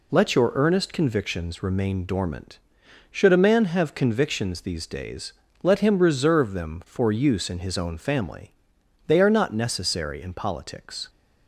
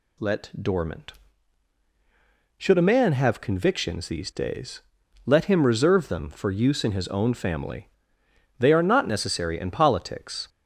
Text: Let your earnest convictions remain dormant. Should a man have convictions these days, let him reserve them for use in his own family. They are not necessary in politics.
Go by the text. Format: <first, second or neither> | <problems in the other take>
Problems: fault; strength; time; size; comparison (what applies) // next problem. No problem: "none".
first | skips "your earnest convictions remain"; at 0.5 s